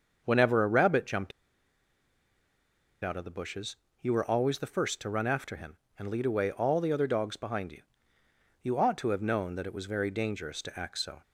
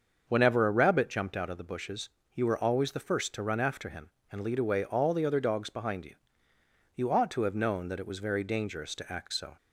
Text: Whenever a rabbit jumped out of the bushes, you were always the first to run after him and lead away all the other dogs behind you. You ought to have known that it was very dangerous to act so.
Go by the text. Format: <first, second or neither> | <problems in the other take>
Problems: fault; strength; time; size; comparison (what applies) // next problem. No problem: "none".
second | starts louder than the rest; until 1.2 s; 6.5 dB; also in the second // pauses between "jumped" and "out"; strong; at 1.3 s; 1.7 s long